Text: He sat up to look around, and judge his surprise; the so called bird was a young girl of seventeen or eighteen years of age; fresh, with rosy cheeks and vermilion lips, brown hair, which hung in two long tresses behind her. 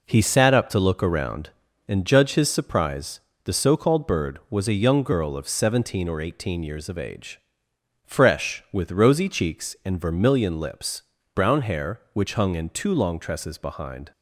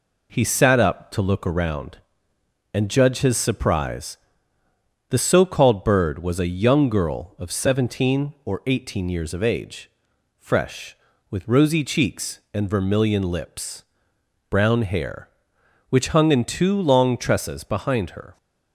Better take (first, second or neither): second